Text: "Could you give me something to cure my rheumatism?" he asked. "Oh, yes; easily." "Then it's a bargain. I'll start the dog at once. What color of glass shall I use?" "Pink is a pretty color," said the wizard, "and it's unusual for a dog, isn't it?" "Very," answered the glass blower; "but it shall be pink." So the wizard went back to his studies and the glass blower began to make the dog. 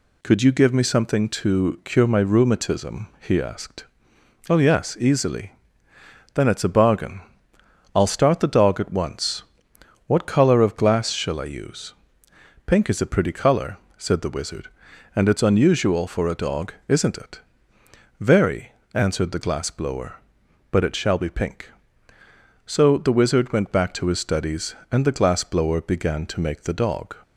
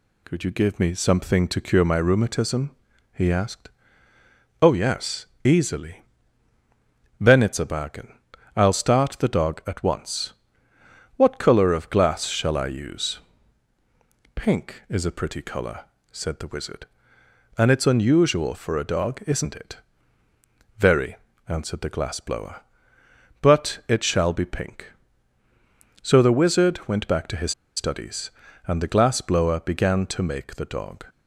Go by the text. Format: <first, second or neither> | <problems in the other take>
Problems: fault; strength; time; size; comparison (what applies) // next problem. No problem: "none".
first | pauses between "his" and "studies"; slight; at 27.5 s; 0.24 s long